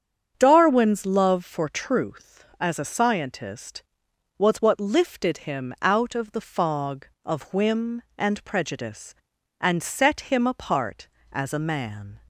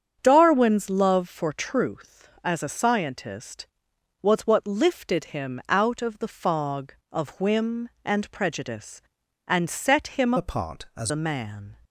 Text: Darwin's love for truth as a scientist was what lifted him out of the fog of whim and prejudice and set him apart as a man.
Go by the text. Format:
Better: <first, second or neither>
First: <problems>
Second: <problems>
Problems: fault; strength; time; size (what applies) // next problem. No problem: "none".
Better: first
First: starts louder than the rest; strong; until 1.3 s; 8 dB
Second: starts louder than the rest; strong; until 1.2 s; 8 dB // changes voice from "apart" to "as"; from 10.3 to 11.1 s; 0.8 s long